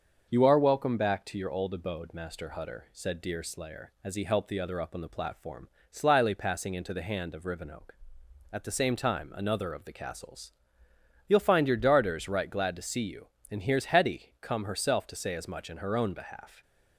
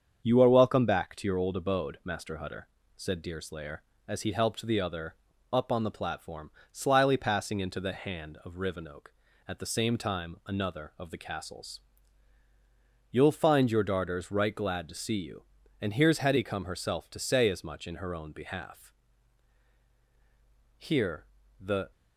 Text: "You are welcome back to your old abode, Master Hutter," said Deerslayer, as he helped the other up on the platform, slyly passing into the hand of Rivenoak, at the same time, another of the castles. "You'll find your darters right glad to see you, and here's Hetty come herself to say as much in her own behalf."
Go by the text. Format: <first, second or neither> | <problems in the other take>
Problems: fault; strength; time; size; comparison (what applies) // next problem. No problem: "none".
first | starts louder than the rest; strong; until 1.2 s; 7 dB; also in the first // pauses between "other" and "up"; slight; at 5.1 s; 0.34 s long // goes on to say "Here the"; noticeable; from 20.7 s on; 1.1 s long